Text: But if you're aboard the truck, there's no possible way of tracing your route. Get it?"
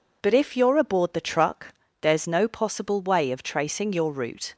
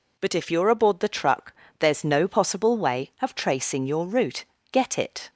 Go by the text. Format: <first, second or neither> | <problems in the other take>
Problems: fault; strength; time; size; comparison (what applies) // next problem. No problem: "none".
second | stops before "Get it"; at 4.5 s